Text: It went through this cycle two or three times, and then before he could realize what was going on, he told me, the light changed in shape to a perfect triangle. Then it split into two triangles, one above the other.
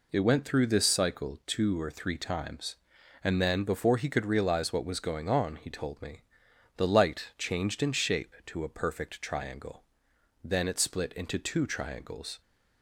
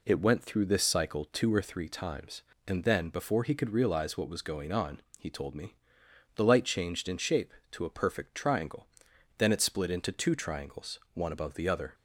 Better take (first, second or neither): second